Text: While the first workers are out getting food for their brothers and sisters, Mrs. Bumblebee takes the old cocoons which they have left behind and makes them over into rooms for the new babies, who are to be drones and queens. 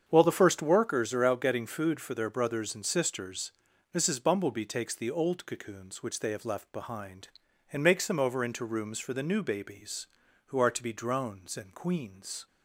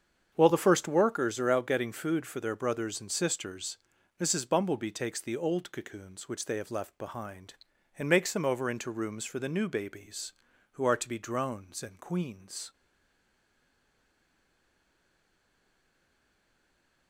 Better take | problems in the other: first | starts louder than the rest; strong; until 1.3 s; 7.5 dB; strong in the first // stays silent after the last word; strong; from 12.7 s on; 4.3 s long

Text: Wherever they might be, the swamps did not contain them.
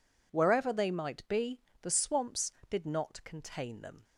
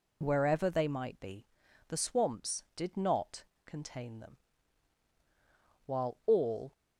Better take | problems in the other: first | goes on to say "While all"; noticeable; from 5.8 s on; 0.86 s long

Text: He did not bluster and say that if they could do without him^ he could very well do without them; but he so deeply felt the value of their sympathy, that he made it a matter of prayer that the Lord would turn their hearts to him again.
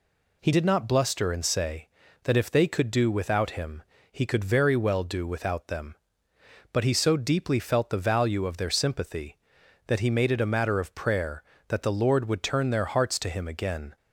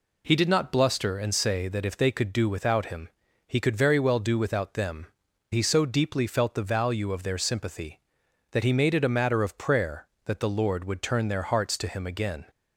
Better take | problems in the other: first | pauses between "him" and "he"; slight; at 3.0 s; 0.36 s long; slight in the first // skips "but"; at 5.2 s

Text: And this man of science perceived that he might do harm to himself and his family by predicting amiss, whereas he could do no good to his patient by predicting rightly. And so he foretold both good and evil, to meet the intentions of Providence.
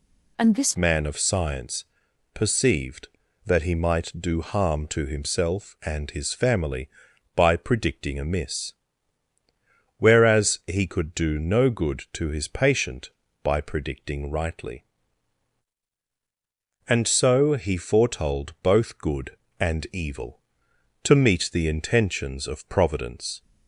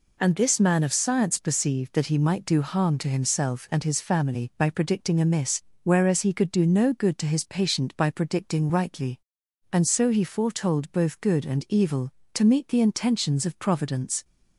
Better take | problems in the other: second | changes voice at "man"; from 0.7 s on; 22.7 s long // pauses between "science" and "perceived"; noticeable; at 1.8 s; 0.50 s long

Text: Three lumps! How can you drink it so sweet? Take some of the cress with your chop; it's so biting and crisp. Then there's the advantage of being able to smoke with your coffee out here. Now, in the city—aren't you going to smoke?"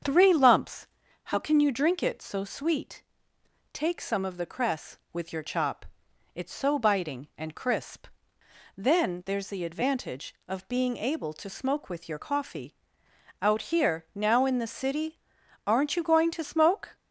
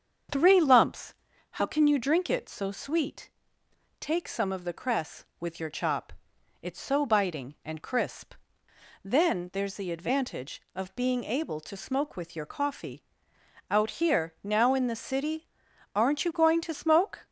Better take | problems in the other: neither | starts louder than the rest; strong; the same in both // pauses between "coffee" and "out"; noticeable; the same in both

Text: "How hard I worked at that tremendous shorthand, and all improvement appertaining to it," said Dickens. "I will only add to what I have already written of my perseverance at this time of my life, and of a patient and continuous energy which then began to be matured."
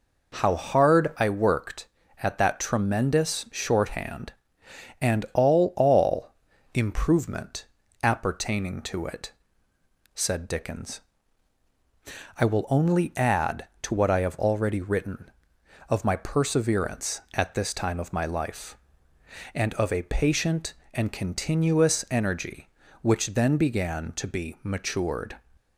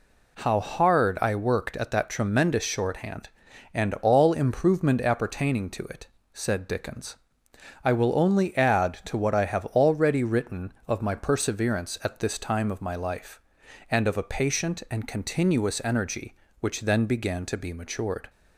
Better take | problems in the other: second | says "all" twice; at 5.7 s // pauses between "improvement" and "appertaining"; slight; at 7.6 s; 0.36 s long

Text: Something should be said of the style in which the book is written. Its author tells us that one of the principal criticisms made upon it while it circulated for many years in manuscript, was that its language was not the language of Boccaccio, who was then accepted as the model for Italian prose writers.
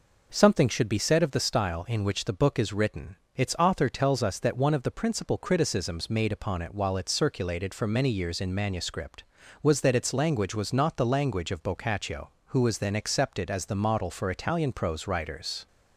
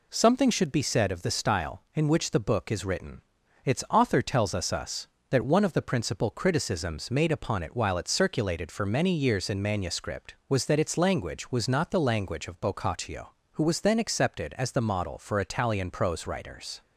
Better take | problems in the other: first | says "us" twice; at 4.7 s

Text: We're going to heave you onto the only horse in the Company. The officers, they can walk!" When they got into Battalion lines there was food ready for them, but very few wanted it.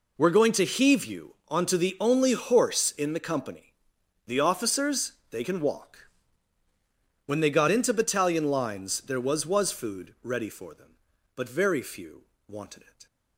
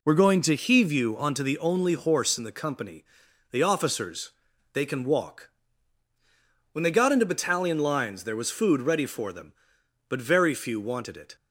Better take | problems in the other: second | pauses between "you" and "onto"; slight; at 1.3 s; 0.16 s long // says "was" twice; at 9.4 s // pauses between "few" and "wanted"; slight; at 12.2 s; 0.22 s long

